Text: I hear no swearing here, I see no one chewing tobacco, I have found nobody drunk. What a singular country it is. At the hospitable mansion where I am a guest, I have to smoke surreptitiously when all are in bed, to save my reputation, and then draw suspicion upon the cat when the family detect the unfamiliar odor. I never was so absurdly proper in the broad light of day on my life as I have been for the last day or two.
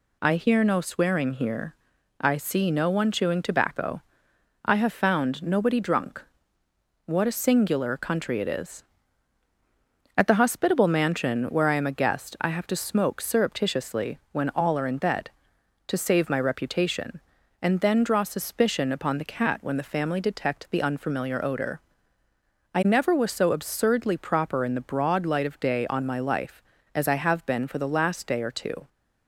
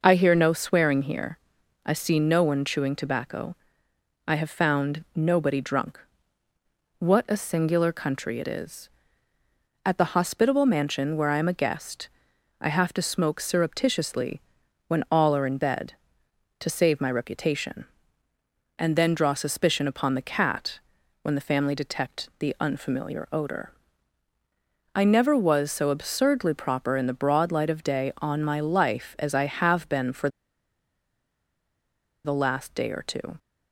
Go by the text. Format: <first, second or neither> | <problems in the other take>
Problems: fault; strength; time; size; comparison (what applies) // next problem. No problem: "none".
first | pauses between "surreptitiously" and "when"; noticeable; at 14.3 s; 0.46 s long // pauses between "cat" and "when"; noticeable; at 20.7 s; 0.46 s long // pauses between "for" and "the"; strong; at 30.2 s; 1.9 s long